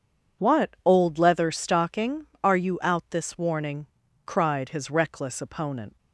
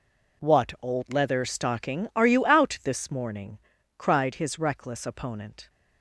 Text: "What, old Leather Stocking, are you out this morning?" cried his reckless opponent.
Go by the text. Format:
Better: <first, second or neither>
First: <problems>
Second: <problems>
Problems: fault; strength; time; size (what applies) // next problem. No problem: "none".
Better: second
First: says "warning" for "morning"; at 3.3 s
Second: none